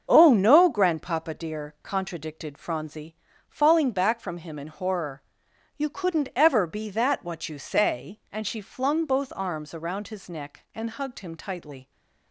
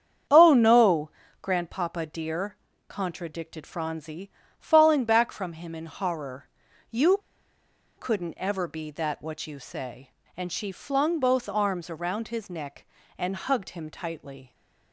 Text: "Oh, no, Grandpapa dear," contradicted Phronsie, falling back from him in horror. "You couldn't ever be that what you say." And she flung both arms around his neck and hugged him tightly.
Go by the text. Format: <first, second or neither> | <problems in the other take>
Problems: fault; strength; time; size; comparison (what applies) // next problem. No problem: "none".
first | starts louder than the rest; strong; until 1.6 s; 8 dB; also in the first // pauses between "You" and "couldn't"; noticeable; at 7.2 s; 0.78 s long